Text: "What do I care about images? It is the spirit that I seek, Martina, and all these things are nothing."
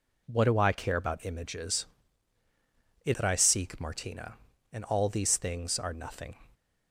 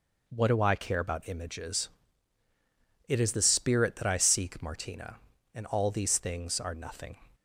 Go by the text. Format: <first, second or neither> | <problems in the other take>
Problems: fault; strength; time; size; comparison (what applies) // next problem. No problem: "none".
second | skips "is the spirit"; at 3.1 s